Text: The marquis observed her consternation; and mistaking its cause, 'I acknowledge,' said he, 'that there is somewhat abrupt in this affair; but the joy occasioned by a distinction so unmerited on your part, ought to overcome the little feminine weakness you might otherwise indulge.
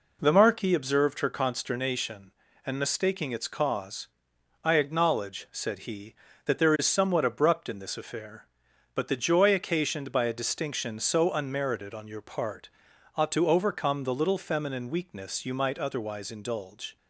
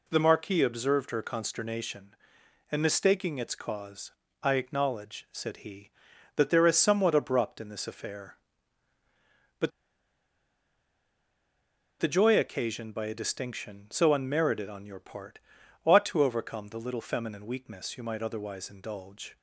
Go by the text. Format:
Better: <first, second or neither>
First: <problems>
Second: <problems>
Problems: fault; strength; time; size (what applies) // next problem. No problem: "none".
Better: first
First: none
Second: pauses between "but" and "the"; strong; at 9.7 s; 2.3 s long